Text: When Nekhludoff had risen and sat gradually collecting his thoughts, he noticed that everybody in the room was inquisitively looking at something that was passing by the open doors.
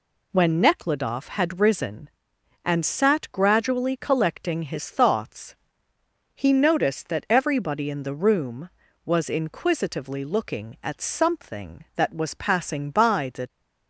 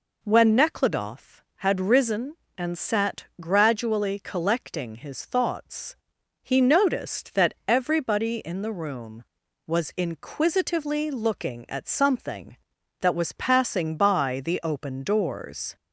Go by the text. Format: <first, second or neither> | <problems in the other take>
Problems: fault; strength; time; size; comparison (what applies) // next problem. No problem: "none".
second | stops before "open doors"; at 13.4 s